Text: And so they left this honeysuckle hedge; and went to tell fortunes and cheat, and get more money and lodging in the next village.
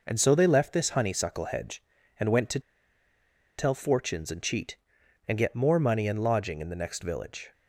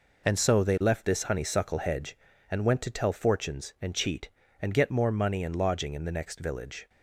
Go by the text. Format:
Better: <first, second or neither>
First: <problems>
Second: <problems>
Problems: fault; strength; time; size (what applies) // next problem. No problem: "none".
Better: second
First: pauses between "to" and "tell"; at 2.5 s; 0.99 s long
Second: none